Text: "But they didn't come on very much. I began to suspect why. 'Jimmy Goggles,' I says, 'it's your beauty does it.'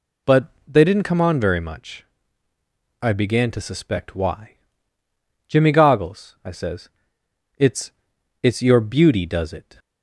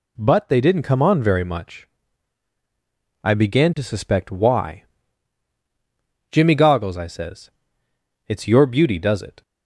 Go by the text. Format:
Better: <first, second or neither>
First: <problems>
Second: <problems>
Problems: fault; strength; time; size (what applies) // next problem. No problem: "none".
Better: second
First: pauses between "But" and "they"; slight; at 0.4 s; 0.18 s long // says "it's" twice; at 8.4 s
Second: none